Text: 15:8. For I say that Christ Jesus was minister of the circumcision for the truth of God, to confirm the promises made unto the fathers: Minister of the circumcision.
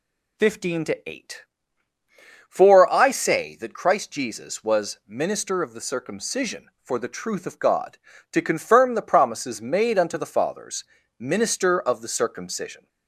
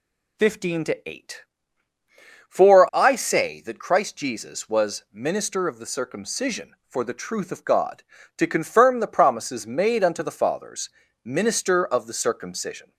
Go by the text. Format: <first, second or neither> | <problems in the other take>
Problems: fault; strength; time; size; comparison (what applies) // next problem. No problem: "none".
neither | none